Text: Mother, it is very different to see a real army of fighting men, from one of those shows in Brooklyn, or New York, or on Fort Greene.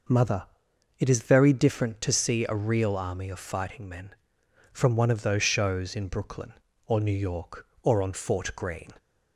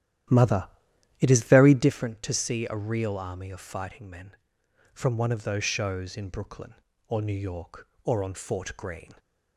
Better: first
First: none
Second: starts louder than the rest; strong; until 1.9 s; 11.5 dB

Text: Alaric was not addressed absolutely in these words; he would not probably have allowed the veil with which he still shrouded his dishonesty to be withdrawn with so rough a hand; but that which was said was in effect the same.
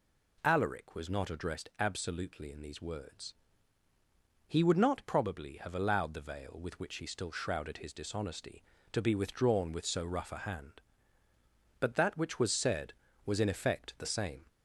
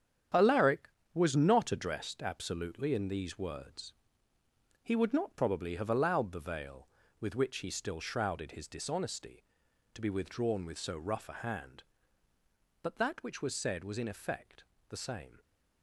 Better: first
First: none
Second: gets quieter; strong; throughout; 8.5 dB // pauses between "effect" and "the"; slight; at 14.6 s; 0.26 s long

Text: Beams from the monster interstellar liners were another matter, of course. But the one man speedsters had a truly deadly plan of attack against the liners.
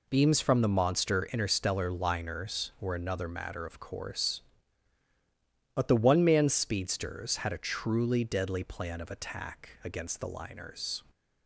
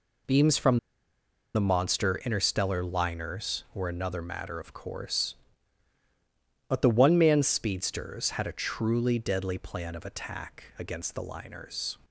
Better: first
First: none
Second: pauses between "from" and "the"; noticeable; at 0.7 s; 0.76 s long

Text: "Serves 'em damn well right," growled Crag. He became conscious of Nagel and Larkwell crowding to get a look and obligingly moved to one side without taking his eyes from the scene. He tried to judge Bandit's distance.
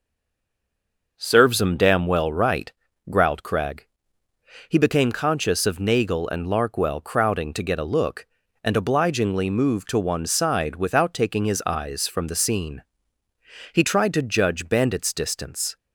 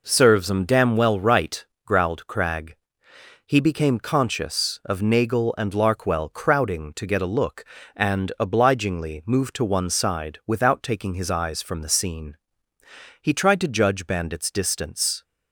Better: second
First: stays silent before the first word; noticeable; until 1.1 s; 1.1 s long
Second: none

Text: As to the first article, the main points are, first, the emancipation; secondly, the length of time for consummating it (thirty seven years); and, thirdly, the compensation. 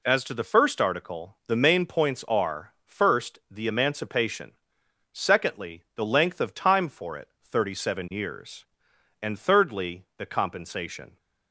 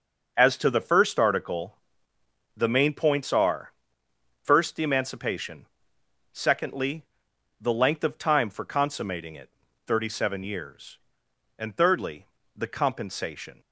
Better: second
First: skips "consummating"; at 7.1 s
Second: none

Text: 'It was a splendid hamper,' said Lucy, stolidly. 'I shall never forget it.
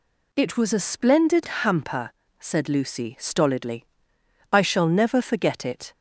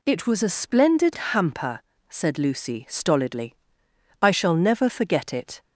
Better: neither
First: none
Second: none

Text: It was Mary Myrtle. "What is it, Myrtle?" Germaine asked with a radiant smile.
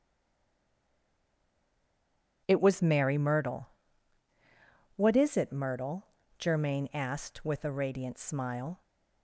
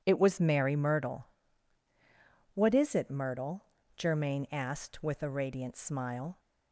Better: second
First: stays silent before the first word; until 2.4 s; 2.4 s long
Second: none

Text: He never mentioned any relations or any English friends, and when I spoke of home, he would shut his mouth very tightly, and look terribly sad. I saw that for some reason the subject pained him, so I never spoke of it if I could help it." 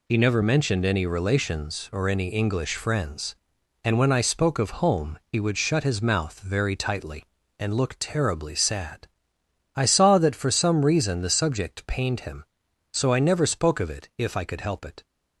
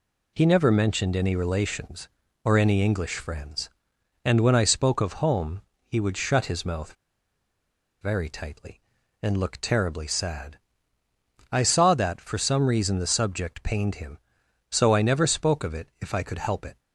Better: first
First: none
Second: pauses between "mouth" and "very"; at 6.9 s; 1.0 s long

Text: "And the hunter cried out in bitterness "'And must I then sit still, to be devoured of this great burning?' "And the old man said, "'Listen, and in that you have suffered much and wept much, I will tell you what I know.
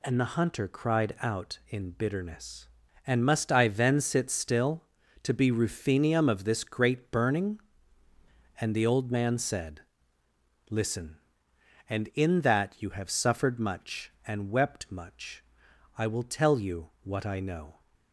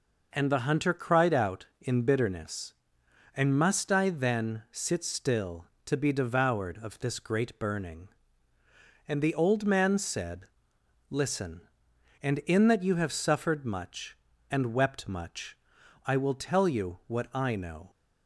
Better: second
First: says "ruthenium" for "devoured"; at 5.5 s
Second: none

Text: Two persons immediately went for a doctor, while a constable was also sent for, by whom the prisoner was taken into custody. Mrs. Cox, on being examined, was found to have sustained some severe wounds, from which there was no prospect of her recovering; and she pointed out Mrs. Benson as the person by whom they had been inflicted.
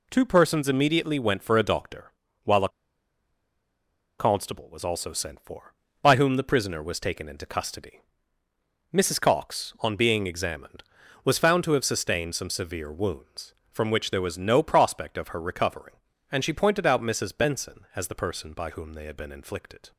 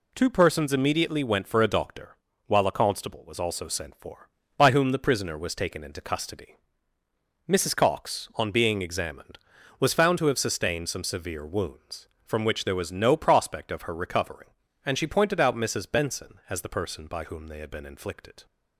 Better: second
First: pauses between "a" and "constable"; strong; at 2.6 s; 1.4 s long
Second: none

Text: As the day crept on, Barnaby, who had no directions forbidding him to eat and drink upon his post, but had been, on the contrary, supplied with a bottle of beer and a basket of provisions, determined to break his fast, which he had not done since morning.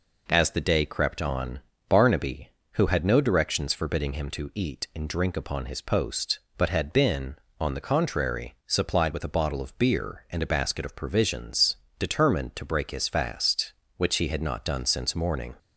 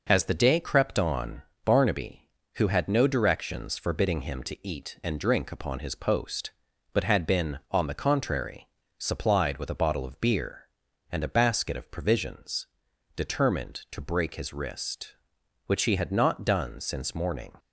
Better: first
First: none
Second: says "wrist" for "fast"; at 14.5 s

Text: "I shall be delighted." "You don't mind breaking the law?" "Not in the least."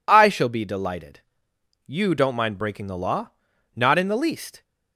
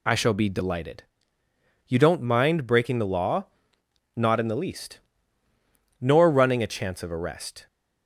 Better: first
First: none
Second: goes on to say "Nor running a chance of arrest"; from 6.0 s on; 1.6 s long

